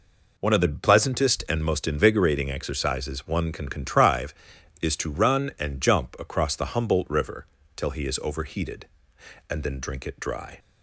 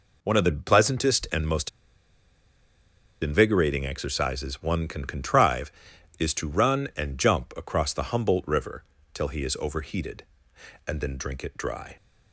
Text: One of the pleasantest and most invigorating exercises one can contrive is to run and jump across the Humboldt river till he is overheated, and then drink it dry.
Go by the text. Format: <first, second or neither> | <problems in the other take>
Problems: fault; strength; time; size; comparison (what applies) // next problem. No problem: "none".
first | pauses between "most" and "invigorating"; strong; at 1.6 s; 1.5 s long // pauses between "river" and "till"; slight; at 8.8 s; 0.30 s long; slight in the first